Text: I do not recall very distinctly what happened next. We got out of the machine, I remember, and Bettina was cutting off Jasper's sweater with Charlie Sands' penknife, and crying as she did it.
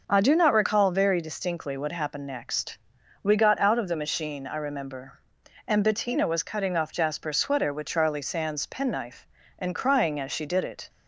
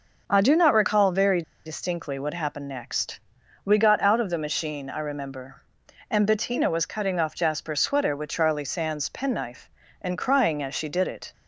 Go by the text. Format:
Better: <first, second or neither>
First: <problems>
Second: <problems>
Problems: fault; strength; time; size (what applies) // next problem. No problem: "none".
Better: first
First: none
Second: pauses between "very" and "distinctly"; slight; at 1.4 s; 0.22 s long